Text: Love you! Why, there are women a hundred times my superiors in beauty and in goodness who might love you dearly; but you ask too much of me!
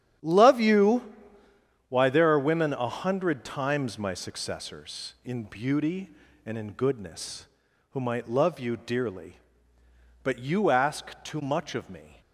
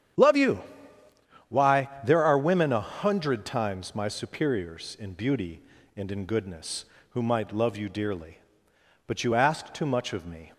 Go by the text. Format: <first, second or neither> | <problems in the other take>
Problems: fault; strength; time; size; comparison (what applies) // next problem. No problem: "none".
second | starts louder than the rest; strong; until 1.9 s; 10 dB; strong in the second // says "successors" for "superiors"; at 4.1 s